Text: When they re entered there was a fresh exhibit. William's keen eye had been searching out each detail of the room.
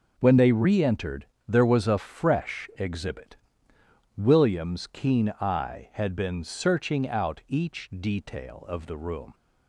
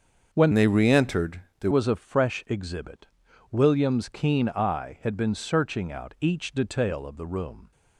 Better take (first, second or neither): first